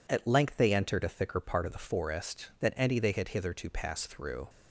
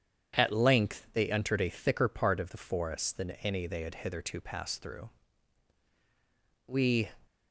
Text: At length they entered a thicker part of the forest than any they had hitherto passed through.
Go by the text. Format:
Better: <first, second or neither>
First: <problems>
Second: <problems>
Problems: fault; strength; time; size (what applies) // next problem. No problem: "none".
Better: first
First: none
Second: goes on to say "We"; slight; from 6.6 s on; 0.44 s long